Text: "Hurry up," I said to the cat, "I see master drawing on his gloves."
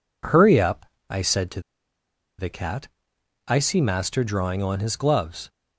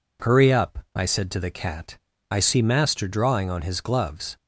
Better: second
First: pauses between "to" and "the"; noticeable; at 1.6 s; 0.78 s long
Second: none

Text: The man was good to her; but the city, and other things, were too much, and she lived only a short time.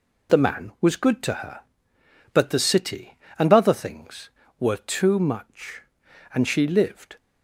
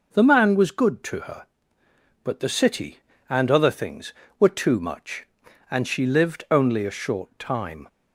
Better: second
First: stops before "only a short time"; at 7.1 s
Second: none

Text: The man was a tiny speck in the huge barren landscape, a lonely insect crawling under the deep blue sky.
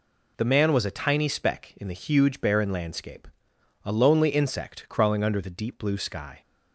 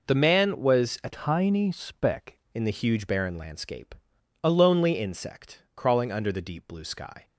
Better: first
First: none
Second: changes voice from "tiny" to "speck"; from 1.1 to 2.3 s; 1.2 s long // pauses between "insect" and "crawling"; slight; at 5.5 s; 0.16 s long

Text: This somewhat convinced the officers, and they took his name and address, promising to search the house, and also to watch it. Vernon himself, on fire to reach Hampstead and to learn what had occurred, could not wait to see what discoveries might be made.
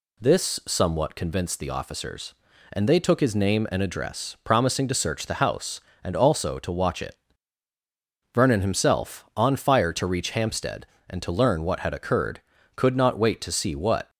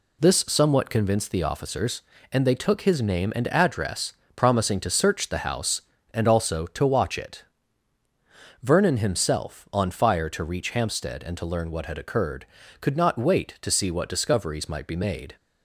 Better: second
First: stops before "discoveries might be made"; at 14.0 s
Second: none

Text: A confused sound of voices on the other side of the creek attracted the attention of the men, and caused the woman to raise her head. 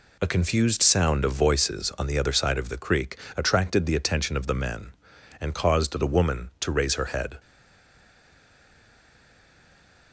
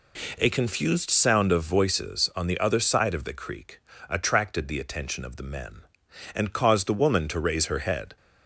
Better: second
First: pauses between "creek" and "attracted"; slight; at 3.1 s; 0.20 s long // stays silent after the last word; strong; from 7.3 s on; 2.8 s long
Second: pauses between "creek" and "attracted"; slight; at 3.8 s; 0.28 s long

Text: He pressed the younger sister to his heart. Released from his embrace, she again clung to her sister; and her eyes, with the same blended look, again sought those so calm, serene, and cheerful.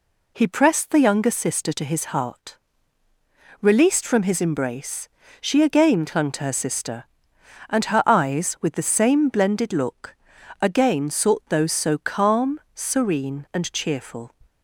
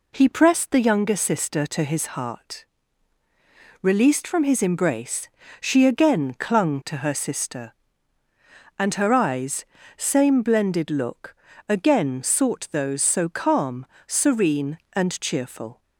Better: first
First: none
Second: skips "with the"; at 9.7 s

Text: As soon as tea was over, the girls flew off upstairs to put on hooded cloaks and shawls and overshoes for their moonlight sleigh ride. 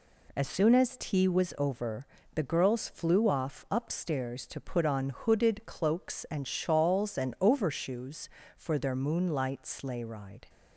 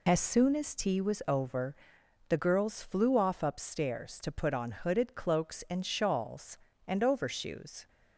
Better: first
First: none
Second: stops before "for their moonlight sleigh ride"; at 7.8 s

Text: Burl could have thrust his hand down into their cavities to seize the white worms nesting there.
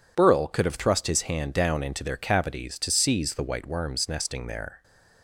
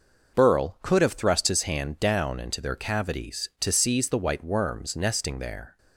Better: neither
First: none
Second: none

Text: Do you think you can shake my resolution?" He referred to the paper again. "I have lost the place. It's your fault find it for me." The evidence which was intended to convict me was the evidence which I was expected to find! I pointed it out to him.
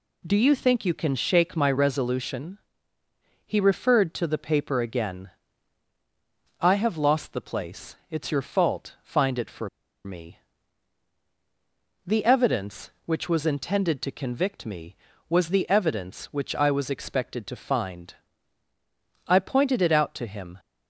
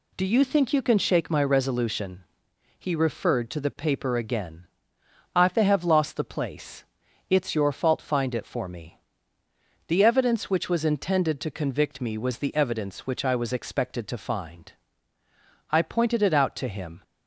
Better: second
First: pauses between "for" and "me"; at 9.6 s; 0.36 s long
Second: none

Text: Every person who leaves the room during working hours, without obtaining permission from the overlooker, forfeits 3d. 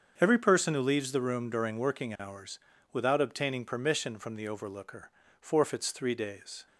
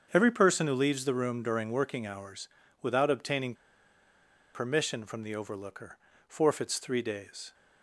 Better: first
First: starts louder than the rest; strong; until 1.1 s; 7 dB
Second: starts louder than the rest; strong; until 1.1 s; 7 dB // pauses between "obtaining" and "permission"; at 3.5 s; 1.0 s long

